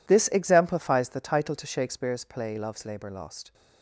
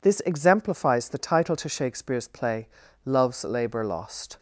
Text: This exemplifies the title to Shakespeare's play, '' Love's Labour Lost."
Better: neither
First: none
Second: none

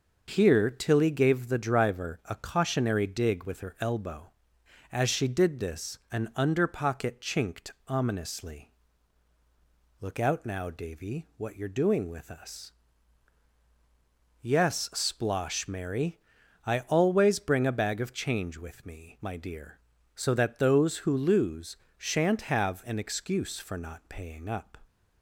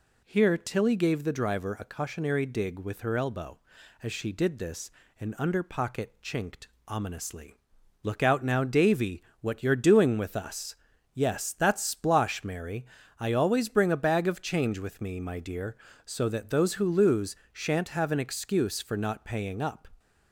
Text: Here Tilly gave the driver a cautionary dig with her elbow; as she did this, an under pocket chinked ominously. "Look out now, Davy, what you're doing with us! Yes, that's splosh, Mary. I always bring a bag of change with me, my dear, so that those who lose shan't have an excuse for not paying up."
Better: second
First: pauses between "chinked" and "ominously"; slight; at 7.7 s; 0.16 s long // skips "that's"; at 14.9 s // pauses between "lose" and "shan't"; slight; at 21.7 s; 0.22 s long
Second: pauses between "chinked" and "ominously"; slight; at 6.6 s; 0.20 s long // pauses between "lose" and "shan't"; slight; at 17.3 s; 0.16 s long

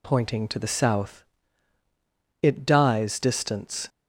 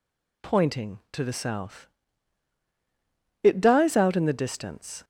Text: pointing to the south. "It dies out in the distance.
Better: second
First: skips "out in the"; at 3.1 s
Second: none

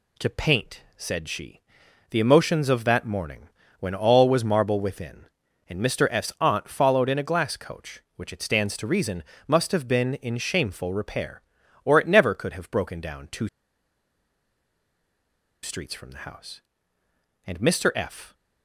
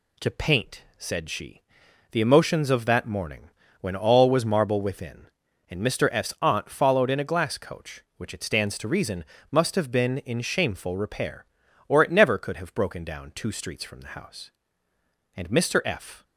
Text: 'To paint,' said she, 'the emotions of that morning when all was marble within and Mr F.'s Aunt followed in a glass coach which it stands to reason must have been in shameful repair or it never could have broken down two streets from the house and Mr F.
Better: second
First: pauses between "morning" and "when"; slight; at 3.4 s; 0.32 s long // pauses between "reason" and "must"; slight; at 9.2 s; 0.26 s long // pauses between "two" and "streets"; strong; at 13.4 s; 2.1 s long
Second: pauses between "morning" and "when"; slight; at 3.4 s; 0.32 s long // pauses between "reason" and "must"; slight; at 9.2 s; 0.28 s long

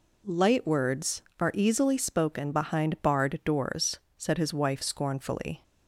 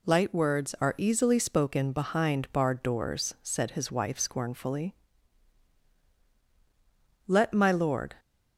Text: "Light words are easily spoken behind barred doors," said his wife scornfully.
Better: first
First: none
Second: goes on to say "Let my lord"; noticeable; from 7.2 s on; 0.92 s long

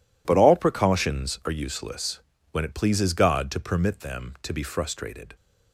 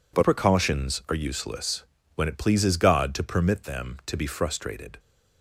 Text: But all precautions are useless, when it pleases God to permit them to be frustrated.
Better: first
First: none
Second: skips "all"; at 0.2 s

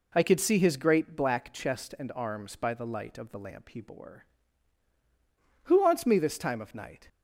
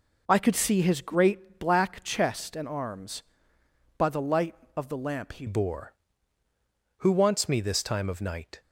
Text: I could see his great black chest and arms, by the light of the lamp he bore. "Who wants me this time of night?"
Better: first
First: none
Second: changes voice at "bore"; from 5.4 s on; 3.2 s long

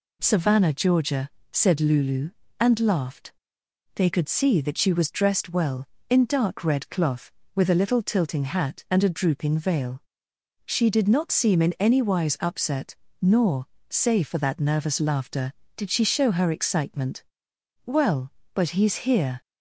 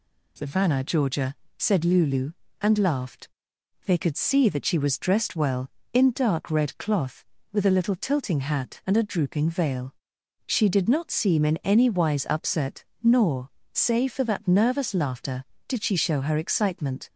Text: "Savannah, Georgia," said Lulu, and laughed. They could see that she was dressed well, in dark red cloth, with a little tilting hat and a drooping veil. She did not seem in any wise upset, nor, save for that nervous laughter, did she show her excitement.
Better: second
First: goes on to say "Well but he's here"; from 17.8 s on; 1.5 s long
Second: none

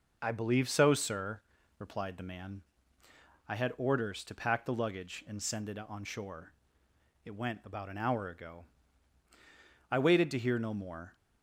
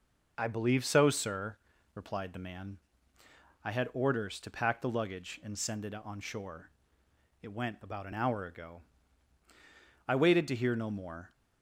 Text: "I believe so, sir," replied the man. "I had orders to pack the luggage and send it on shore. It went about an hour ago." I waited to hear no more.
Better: neither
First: none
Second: none

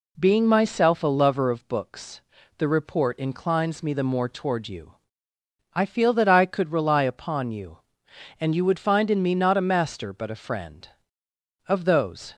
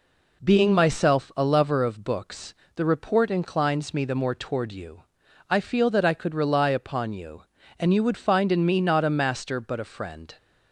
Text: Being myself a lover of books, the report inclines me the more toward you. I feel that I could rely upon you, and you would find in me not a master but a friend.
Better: second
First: goes on to say "Of those"; noticeable; from 11.6 s on; 0.68 s long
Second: none

